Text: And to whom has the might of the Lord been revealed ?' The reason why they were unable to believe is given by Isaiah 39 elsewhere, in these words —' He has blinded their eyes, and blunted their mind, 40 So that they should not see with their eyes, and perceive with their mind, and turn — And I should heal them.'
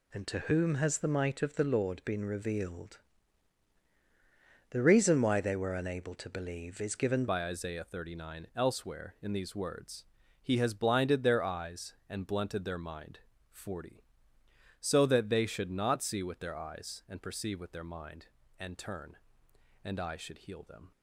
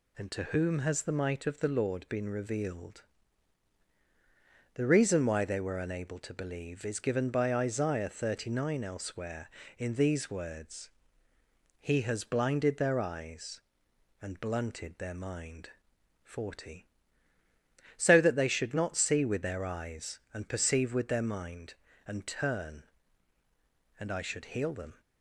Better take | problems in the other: second | changes voice at "by"; from 7.2 s on; 13.7 s long

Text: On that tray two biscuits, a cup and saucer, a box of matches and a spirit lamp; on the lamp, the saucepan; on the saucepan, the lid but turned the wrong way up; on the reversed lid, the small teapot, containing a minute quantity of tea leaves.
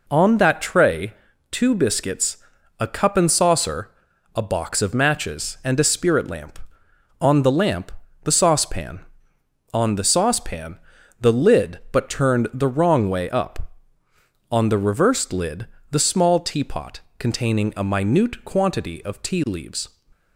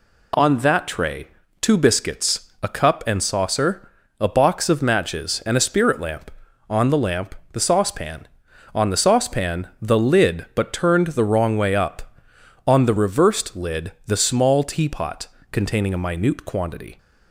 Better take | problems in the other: first | pauses between "tray" and "two"; slight; at 1.2 s; 0.32 s long; also in the first // stops before "of tea leaves"; at 16.9 s

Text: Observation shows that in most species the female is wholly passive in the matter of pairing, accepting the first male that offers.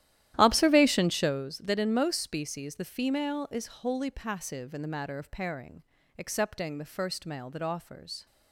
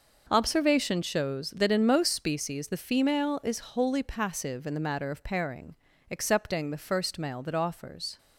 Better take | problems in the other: second | starts louder than the rest; strong; until 1.5 s; 12.5 dB

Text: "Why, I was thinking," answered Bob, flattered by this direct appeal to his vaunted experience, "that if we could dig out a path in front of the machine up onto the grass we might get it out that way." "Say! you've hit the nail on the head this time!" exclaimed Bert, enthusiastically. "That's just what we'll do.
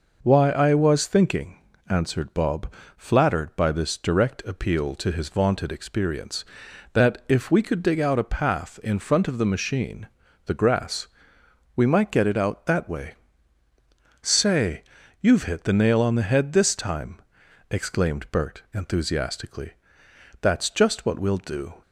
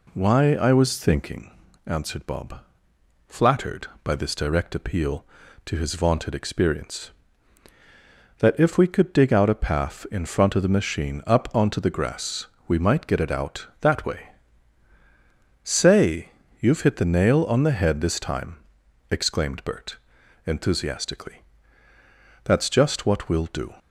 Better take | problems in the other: second | skips "up onto"; at 10.2 s // pauses between "grass" and "we"; noticeable; at 11.0 s; 0.68 s long; slight in the second

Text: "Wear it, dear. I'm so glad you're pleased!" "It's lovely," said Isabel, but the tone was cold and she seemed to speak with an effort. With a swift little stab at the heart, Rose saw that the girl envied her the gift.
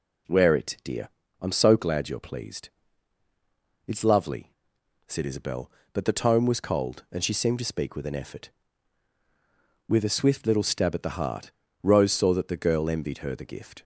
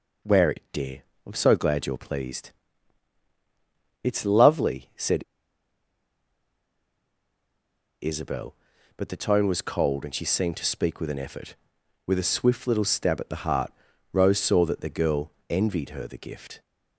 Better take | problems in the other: first | pauses between "said" and "Isabel"; strong; at 5.2 s; 2.7 s long // pauses between "girl" and "envied"; slight; at 15.3 s; 0.18 s long

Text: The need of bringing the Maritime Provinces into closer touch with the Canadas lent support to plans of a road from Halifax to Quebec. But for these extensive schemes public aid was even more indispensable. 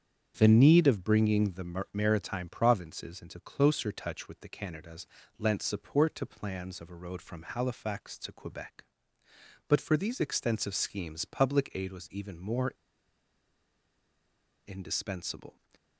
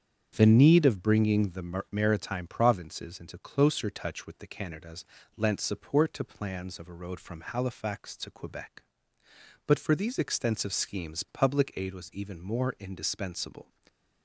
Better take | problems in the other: second | starts louder than the rest; strong; until 1.4 s; 7.5 dB; strong in the second // pauses between "Canadas" and "lent"; slight; at 5.0 s; 0.32 s long; slight in the second // pauses between "more" and "indispensable"; strong; at 12.7 s; 1.9 s long

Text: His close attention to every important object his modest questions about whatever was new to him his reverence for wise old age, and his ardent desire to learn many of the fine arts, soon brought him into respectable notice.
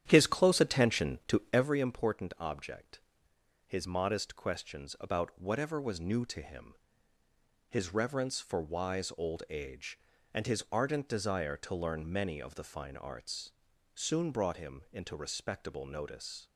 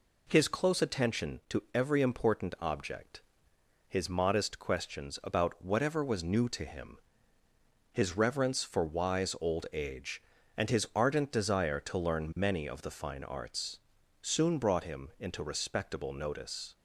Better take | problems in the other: second | starts louder than the rest; strong; until 1.7 s; 10 dB // pauses between "object" and "his"; noticeable; at 3.0 s; 0.66 s long; noticeable in the second // pauses between "him" and "his"; noticeable; at 6.7 s; 0.96 s long; noticeable in the second

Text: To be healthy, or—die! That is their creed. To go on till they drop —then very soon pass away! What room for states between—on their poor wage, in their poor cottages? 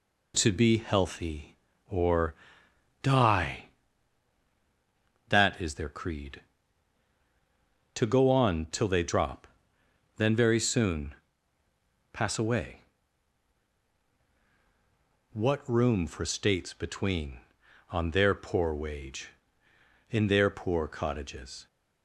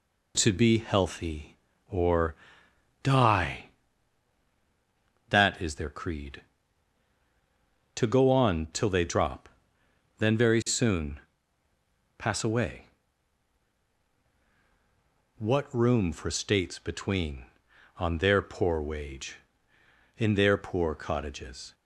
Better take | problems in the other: neither | pauses between "soon" and "pass"; noticeable; the same in both

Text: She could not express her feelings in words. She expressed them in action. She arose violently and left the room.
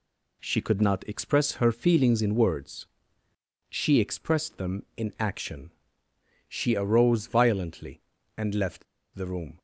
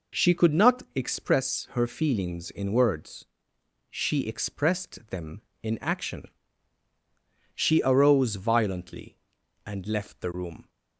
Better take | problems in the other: second | pauses between "left" and "the"; slight; at 8.8 s; 0.30 s long

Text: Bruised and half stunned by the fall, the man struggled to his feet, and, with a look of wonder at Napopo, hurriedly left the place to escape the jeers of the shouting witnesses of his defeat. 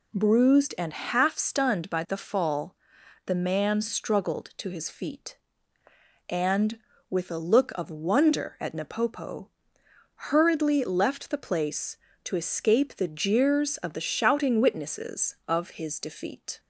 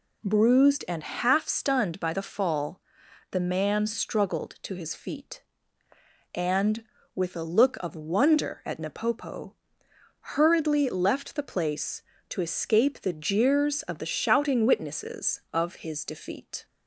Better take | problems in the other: neither | none

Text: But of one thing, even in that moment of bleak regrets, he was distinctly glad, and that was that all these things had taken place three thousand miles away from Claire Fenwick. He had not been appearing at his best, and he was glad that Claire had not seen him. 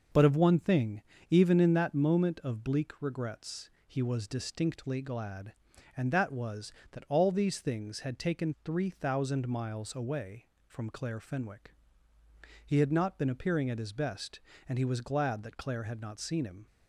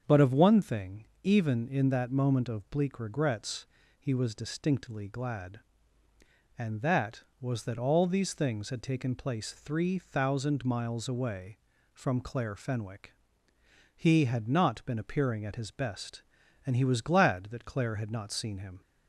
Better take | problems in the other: second | starts louder than the rest; until 1.4 s; 6.5 dB; also in the second // skips "place"; at 8.5 s

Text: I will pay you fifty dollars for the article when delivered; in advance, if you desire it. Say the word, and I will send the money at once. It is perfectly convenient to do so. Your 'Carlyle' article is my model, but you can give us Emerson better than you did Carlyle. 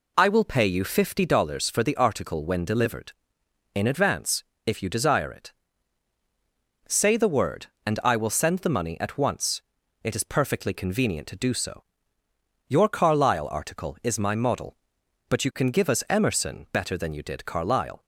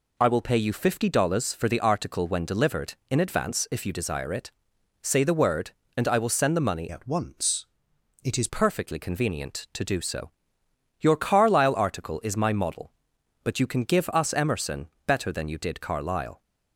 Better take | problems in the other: first | changes voice from "at" to "is"; from 6.9 to 8.4 s; 1.5 s long // pauses between "Emerson" and "better"; slight; at 14.8 s; 0.18 s long

